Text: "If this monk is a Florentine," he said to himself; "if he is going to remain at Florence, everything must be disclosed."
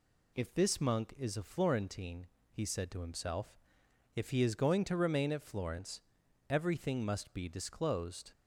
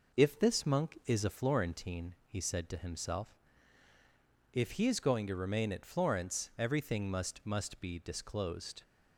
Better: first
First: none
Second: says "must" twice; at 7.4 s

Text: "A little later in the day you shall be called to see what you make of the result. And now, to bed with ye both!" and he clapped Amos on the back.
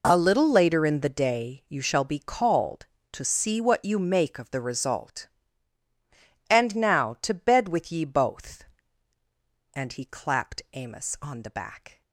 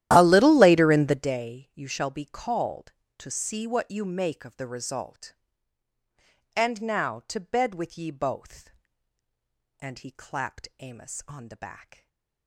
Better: first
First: none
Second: starts louder than the rest; strong; until 1.4 s; 13 dB // stays silent after the last word; slight; from 11.9 s on; 0.5 s long

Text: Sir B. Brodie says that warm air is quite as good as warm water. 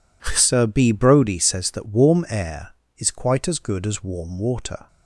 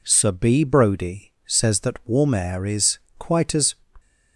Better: first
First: none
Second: pauses between "is" and "quite"; slight; at 2.9 s; 0.20 s long // stops before "good as warm water"; at 3.9 s

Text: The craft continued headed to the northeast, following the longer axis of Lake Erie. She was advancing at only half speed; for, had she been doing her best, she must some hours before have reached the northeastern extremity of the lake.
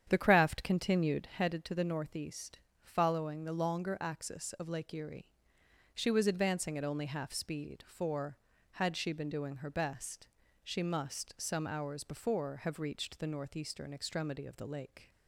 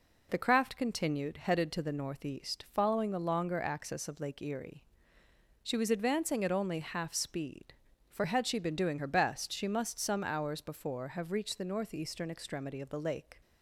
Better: second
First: starts louder than the rest; strong; until 1.4 s; 9 dB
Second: none

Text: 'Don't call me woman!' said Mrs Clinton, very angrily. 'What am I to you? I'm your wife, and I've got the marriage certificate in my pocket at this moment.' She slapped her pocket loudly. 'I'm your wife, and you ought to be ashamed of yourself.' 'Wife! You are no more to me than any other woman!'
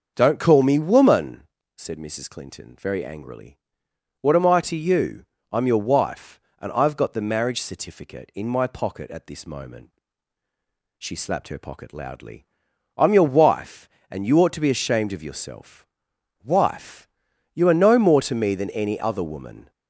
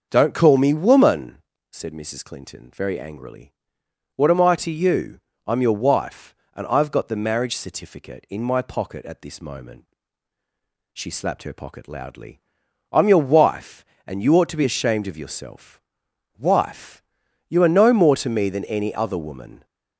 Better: neither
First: starts louder than the rest; until 1.1 s; 6.5 dB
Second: starts louder than the rest; until 1.1 s; 6.5 dB

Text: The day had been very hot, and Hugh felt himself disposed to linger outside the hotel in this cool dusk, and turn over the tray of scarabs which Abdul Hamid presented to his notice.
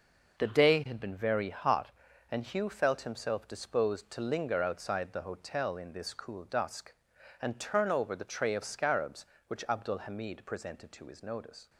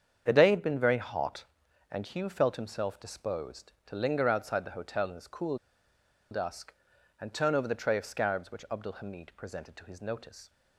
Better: first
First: none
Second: starts louder than the rest; strong; until 1.2 s; 7.5 dB // pauses between "cool" and "dusk"; noticeable; at 5.5 s; 0.74 s long

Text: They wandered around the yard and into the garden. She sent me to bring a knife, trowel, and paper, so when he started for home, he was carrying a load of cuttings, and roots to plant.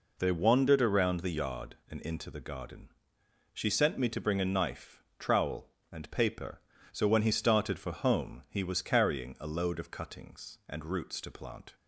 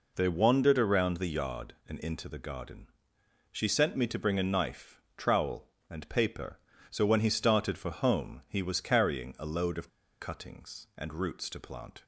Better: first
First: none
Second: pauses between "of" and "cuttings"; slight; at 9.8 s; 0.30 s long

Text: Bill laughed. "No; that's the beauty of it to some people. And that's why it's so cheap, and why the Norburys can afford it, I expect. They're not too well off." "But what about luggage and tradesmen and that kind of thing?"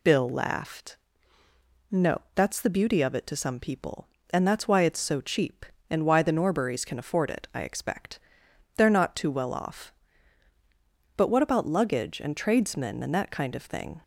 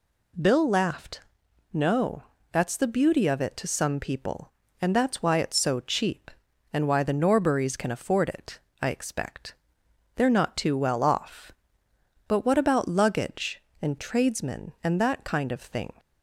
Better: neither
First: none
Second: none

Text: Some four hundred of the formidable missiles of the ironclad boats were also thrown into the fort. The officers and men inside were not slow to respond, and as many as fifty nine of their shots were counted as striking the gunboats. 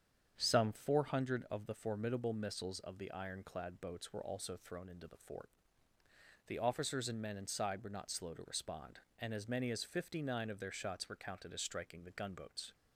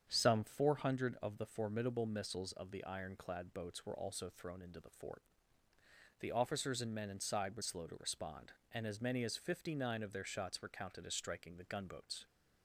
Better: first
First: starts louder than the rest; strong; until 1.3 s; 8 dB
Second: starts louder than the rest; strong; until 1.1 s; 8 dB // skips "not"; at 7.6 s

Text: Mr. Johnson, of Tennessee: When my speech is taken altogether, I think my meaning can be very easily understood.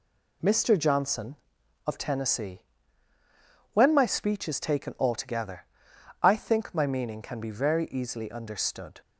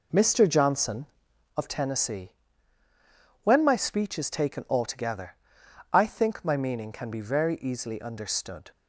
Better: first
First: none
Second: starts louder than the rest; noticeable; until 1.6 s; 4.5 dB

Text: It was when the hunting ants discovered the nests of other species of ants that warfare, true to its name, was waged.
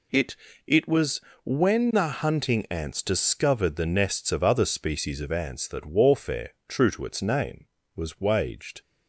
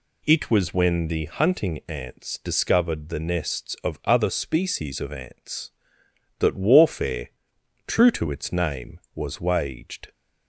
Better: second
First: says "It" twice; at 0.6 s // pauses between "was" and "when"; slight; at 1.1 s; 0.24 s long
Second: none

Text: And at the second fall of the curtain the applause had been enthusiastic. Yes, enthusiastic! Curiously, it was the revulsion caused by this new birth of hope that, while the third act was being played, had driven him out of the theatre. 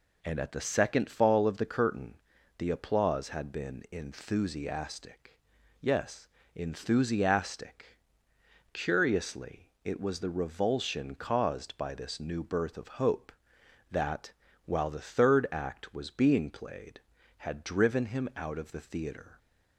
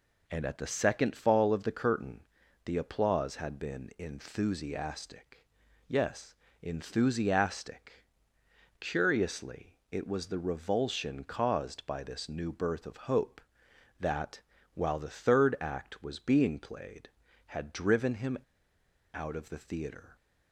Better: first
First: pauses between "curtain" and "the"; at 2.1 s; 0.39 s long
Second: pauses between "curtain" and "the"; at 2.2 s; 0.40 s long // pauses between "him" and "out"; noticeable; at 18.3 s; 0.76 s long

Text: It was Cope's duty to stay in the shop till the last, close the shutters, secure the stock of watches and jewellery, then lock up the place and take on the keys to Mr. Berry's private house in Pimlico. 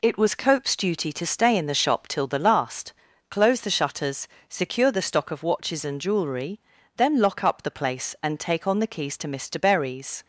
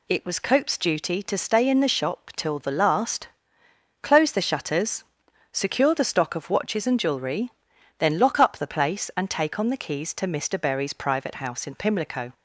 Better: second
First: stops before "private house in Pimlico"; at 10.2 s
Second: none

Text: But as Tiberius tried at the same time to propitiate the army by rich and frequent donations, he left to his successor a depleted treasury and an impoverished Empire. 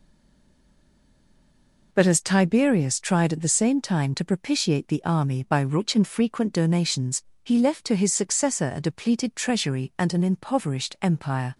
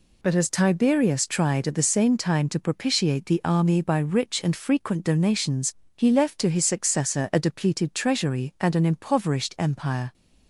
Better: second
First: stays silent before the first word; noticeable; until 1.9 s; 1.9 s long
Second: none

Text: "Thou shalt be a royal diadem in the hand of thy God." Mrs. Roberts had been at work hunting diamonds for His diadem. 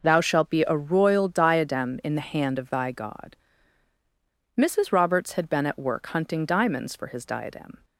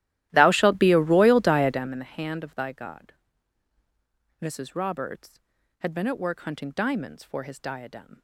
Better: first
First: none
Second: starts louder than the rest; strong; until 2.0 s; 14.5 dB

